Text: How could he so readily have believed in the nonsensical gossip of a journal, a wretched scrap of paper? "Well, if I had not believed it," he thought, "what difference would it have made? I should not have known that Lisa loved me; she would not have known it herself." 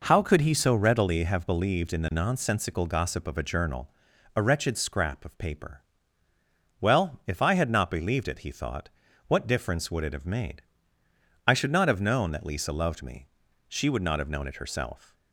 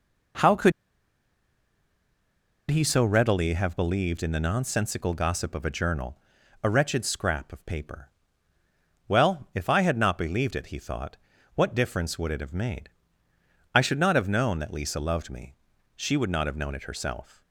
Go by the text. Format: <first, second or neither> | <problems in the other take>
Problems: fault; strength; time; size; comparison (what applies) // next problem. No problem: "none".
first | pauses between "could" and "he"; strong; at 0.7 s; 1.9 s long